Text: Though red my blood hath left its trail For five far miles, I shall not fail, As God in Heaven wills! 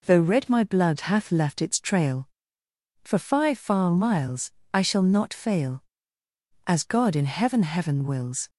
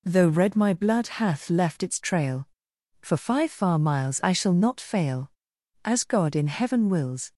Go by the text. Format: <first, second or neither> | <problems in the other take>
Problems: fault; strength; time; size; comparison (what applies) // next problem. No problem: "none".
second | says "Heaven" twice; at 7.6 s